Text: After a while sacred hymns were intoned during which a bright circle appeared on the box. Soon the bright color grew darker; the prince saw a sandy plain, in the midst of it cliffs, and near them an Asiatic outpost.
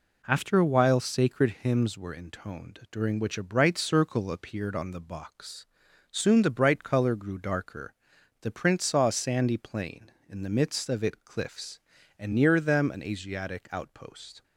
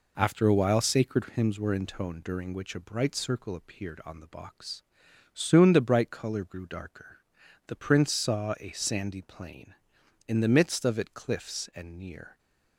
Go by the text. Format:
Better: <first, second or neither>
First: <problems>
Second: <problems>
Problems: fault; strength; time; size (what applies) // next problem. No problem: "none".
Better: first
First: none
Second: stops before "them an Asiatic outpost"; at 12.3 s